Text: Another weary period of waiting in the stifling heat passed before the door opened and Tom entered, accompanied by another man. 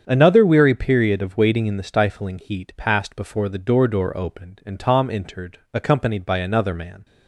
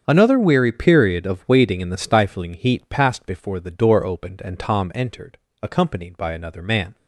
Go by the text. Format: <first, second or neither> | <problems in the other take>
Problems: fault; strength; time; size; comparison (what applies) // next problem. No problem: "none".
second | starts louder than the rest; strong; until 1.0 s; 7.5 dB; strong in the second // says "door" twice; at 3.8 s